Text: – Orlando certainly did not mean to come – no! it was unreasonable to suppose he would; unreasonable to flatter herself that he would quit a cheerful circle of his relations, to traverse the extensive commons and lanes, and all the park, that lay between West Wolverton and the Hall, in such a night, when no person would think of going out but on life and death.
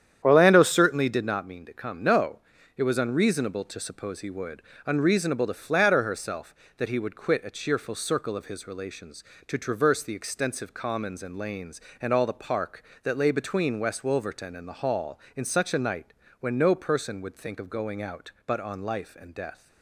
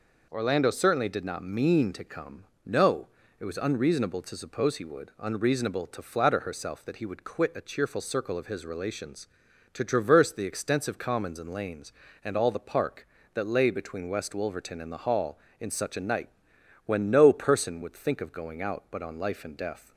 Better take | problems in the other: second | starts louder than the rest; strong; until 1.3 s; 9.5 dB

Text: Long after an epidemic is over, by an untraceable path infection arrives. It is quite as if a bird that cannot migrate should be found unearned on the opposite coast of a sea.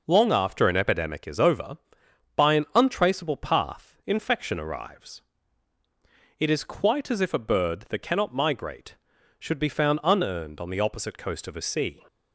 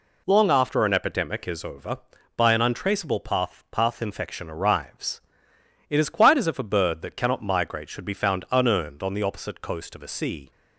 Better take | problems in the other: first | says "path" twice; at 3.7 s

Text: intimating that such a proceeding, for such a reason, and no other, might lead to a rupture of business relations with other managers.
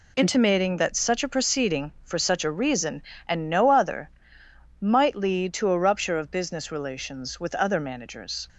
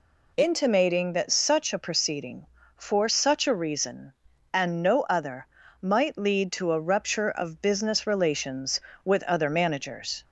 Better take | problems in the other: neither | none

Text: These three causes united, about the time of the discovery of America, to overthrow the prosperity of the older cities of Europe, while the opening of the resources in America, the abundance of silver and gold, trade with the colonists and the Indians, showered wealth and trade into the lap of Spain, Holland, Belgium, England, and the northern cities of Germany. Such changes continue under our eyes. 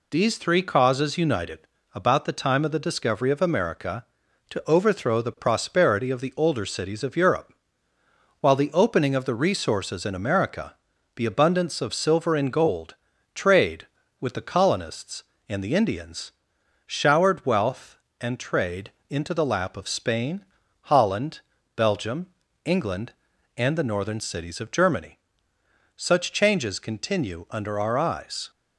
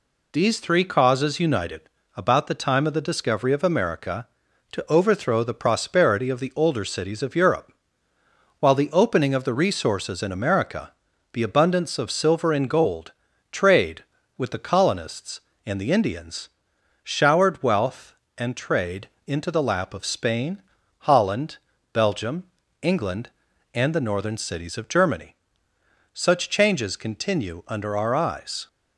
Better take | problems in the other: neither | pauses between "trade" and "into"; slight; the same in both

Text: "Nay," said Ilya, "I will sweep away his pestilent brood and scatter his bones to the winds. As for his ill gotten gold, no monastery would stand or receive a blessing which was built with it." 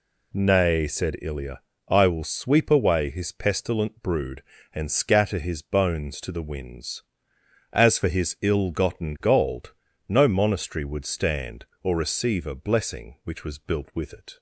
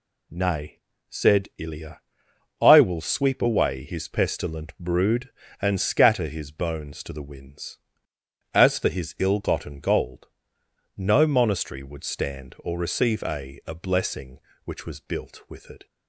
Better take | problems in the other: first | says "a" twice; at 13.6 s

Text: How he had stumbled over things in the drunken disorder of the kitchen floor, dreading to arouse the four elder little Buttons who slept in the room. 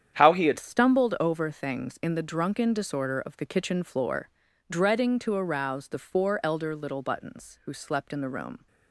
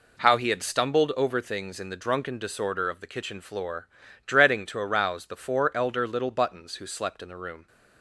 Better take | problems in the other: second | starts louder than the rest; strong; until 1.1 s; 9.5 dB // changes voice at "stumbled"; from 0.5 s on; 8.1 s long

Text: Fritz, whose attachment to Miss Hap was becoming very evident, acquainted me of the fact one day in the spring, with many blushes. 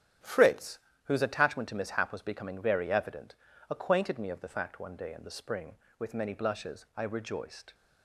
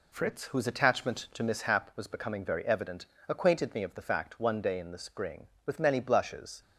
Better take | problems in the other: second | starts louder than the rest; strong; until 1.4 s; 9.5 dB // goes on to say "I rejoiced"; noticeable; from 6.9 s on; 0.78 s long

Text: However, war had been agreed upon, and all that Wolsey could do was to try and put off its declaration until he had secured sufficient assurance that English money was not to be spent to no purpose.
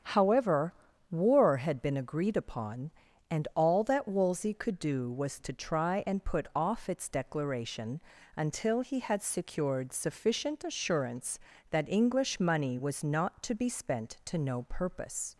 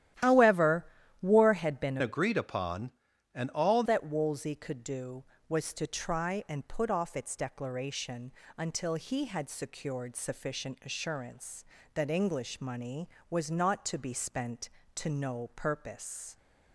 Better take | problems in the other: first | starts louder than the rest; strong; until 1.5 s; 12.5 dB; strong in the first // changes voice from "agreed" to "all"; from 2.0 to 3.8 s; 1.8 s long // pauses between "declaration" and "until"; slight; at 8.3 s; 0.24 s long; slight in the first

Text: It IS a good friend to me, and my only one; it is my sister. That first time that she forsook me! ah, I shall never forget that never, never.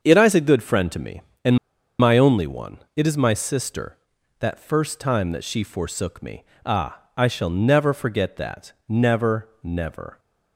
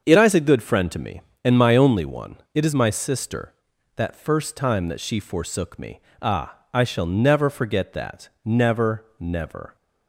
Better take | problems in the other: second | starts louder than the rest; until 1.0 s; 7 dB; also in the second // pauses between "and" and "my"; at 1.5 s; 0.43 s long // pauses between "that" and "never"; slight; at 8.7 s; 0.16 s long; slight in the second

